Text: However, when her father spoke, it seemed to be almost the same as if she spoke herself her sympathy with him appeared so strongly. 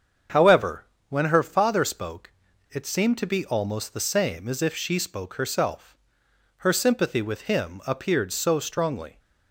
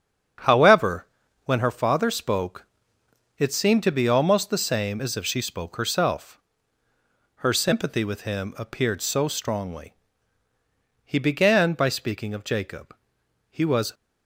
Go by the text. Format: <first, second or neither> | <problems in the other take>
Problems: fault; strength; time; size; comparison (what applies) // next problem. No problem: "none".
first | starts louder than the rest; strong; until 1.8 s; 7.5 dB; strong in the first // pauses between "herself" and "her"; at 6.3 s; 1.0 s long; noticeable in the first // goes on to say "He began by speaking of Jacob he was"; strong; from 11.0 s on; 2.9 s long